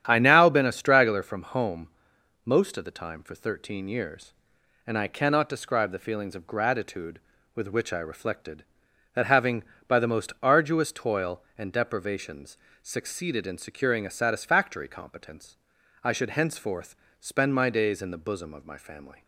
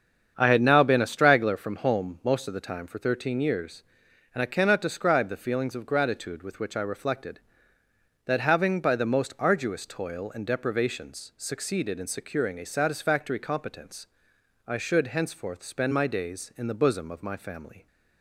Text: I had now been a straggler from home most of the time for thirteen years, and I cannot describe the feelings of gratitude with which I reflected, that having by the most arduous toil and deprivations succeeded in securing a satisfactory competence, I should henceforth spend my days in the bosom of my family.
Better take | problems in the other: second | starts louder than the rest; strong; until 1.0 s; 10 dB; strong in the second // skips "had"; at 0.1 s // pauses between "home" and "most"; noticeable; at 1.8 s; 0.56 s long // pauses between "deprivations" and "succeeded"; slight; at 12.5 s; 0.24 s long // pauses between "henceforth" and "spend"; slight; at 16.9 s; 0.24 s long

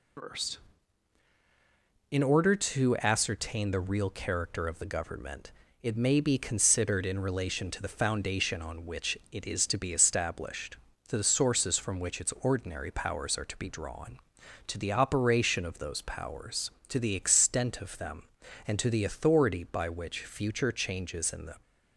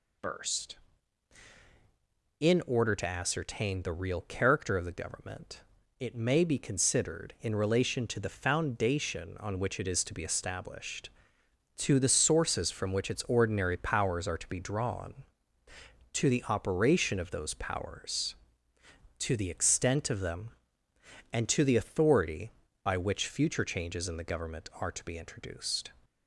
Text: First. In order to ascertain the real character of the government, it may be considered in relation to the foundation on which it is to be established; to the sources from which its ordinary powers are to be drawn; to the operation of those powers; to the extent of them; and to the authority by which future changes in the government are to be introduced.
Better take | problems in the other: second | stops before "government are to be introduced"; at 21.6 s

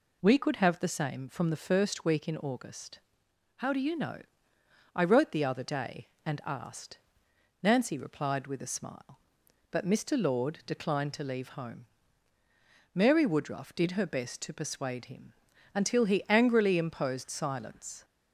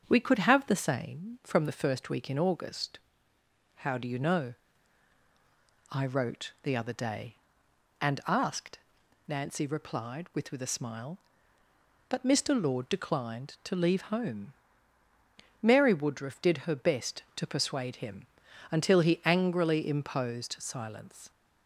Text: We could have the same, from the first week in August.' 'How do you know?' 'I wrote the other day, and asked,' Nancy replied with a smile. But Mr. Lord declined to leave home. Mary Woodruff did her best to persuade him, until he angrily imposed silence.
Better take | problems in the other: first | starts louder than the rest; until 1.1 s; 7 dB // says "with" twice; at 10.5 s

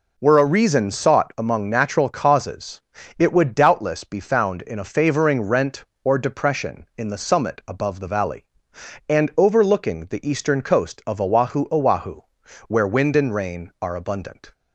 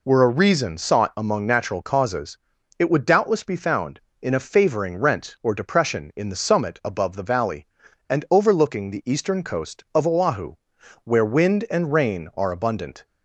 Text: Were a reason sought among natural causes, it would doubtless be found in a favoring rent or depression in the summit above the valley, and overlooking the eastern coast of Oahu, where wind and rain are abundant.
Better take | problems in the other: second | says "Oahu" twice; at 11.6 s

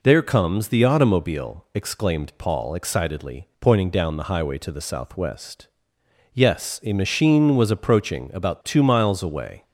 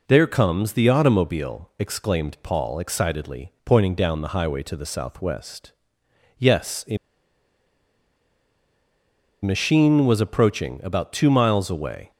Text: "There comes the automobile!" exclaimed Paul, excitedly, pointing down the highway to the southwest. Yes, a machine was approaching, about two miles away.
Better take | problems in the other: first | pauses between "a" and "machine"; strong; at 6.9 s; 2.4 s long

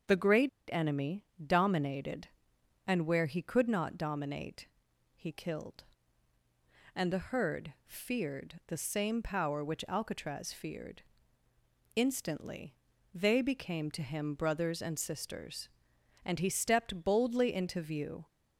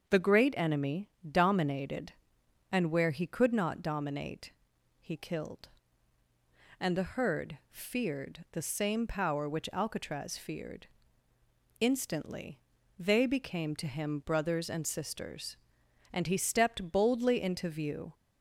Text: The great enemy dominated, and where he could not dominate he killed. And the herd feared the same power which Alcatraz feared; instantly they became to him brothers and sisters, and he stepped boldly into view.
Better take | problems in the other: second | starts louder than the rest; until 1.5 s; 7 dB; also in the second // pauses between "great" and "enemy"; slight; at 0.4 s; 0.21 s long // pauses between "enemy" and "dominated"; slight; at 1.2 s; 0.20 s long; slight in the second // pauses between "dominate" and "he"; noticeable; at 4.6 s; 0.48 s long; noticeable in the second // pauses between "instantly" and "they"; slight; at 12.7 s; 0.36 s long; slight in the second

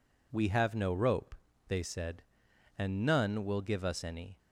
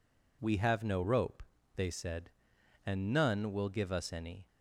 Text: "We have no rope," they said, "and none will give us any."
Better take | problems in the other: neither | none

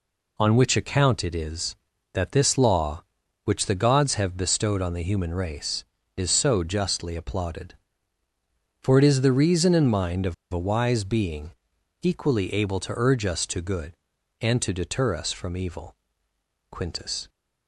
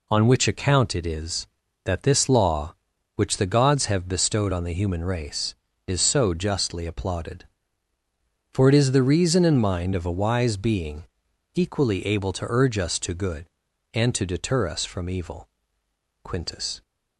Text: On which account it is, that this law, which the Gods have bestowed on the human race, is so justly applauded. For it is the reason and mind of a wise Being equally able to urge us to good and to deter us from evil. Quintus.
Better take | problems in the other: second | pauses between "of" and "a"; slight; at 10.3 s; 0.18 s long // pauses between "Being" and "equally"; noticeable; at 11.5 s; 0.50 s long; noticeable in the second

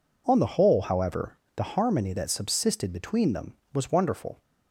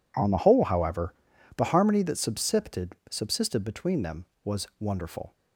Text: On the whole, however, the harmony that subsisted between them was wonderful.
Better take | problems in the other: first | says "subsisted" twice; at 3.0 s

